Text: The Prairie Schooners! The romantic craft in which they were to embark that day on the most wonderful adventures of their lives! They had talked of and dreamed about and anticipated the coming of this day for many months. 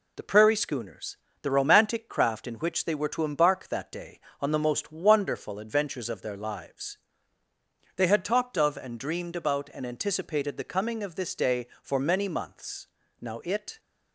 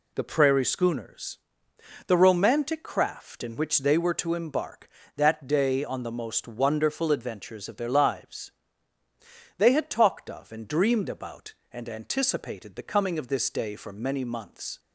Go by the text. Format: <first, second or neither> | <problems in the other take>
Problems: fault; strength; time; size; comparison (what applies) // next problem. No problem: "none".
second | goes on to say "Now it"; from 13.2 s on; 0.58 s long